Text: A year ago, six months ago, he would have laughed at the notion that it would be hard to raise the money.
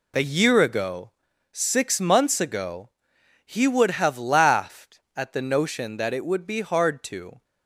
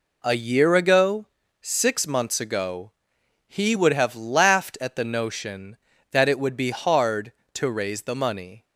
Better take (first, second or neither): second